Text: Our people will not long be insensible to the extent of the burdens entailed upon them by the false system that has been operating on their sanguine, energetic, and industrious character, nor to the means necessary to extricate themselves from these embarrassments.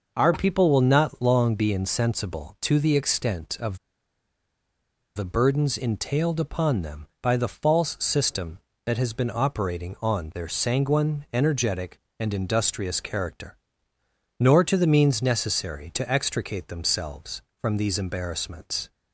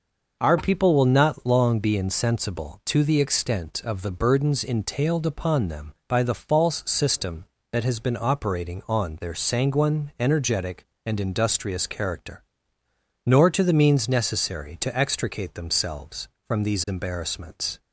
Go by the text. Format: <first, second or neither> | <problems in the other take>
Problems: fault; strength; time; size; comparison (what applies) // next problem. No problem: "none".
second | pauses between "of" and "the"; strong; at 3.7 s; 1.3 s long